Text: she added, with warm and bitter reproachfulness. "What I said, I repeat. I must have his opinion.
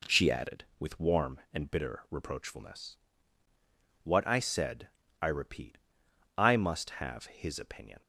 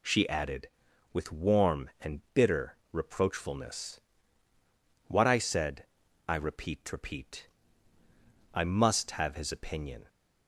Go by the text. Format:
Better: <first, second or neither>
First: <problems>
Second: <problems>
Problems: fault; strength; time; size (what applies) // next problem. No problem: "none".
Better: first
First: none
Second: pauses between "bitter" and "reproachfulness"; slight; at 2.7 s; 0.16 s long // says "repeat" twice; at 6.9 s